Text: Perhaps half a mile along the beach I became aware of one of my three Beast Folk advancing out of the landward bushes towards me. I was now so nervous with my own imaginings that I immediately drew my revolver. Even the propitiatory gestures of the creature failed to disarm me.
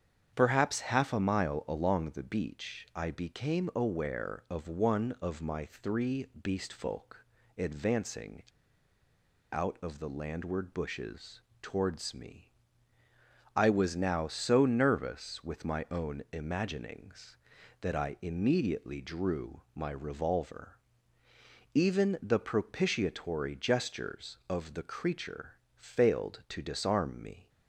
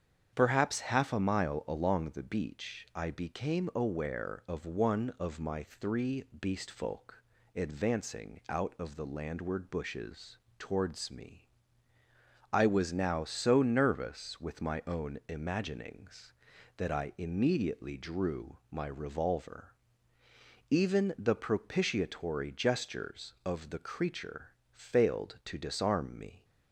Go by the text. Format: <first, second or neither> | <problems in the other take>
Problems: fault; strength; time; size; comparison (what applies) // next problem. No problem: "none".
second | starts louder than the rest; strong; until 1.3 s; 8 dB; strong in the second // pauses between "three" and "Beast"; slight; at 6.2 s; 0.16 s long; slight in the second // pauses between "Folk" and "advancing"; slight; at 7.2 s; 0.32 s long; slight in the second // pauses between "advancing" and "out"; at 8.4 s; 1.1 s long // pauses between "bushes" and "towards"; slight; at 11.4 s; 0.20 s long; slight in the second // pauses between "creature" and "failed"; slight; at 25.5 s; 0.20 s long; slight in the second